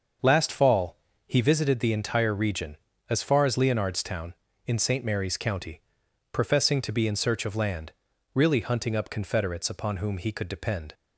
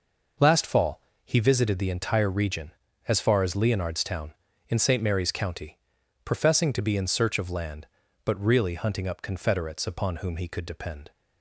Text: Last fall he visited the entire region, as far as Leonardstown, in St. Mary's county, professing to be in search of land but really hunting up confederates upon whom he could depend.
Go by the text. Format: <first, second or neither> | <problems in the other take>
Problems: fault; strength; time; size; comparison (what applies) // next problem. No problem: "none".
second | starts louder than the rest; until 1.5 s; 6.5 dB // pauses between "fall" and "he"; slight; at 0.9 s; 0.28 s long; slight in the second // skips "but"; at 8.1 s